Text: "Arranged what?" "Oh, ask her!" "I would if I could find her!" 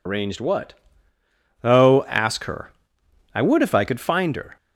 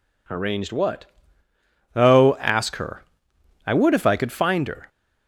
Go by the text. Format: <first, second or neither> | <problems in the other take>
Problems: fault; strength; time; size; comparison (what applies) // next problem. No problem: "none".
second | loses the start of "Arranged"; at 0.0 s; 90 ms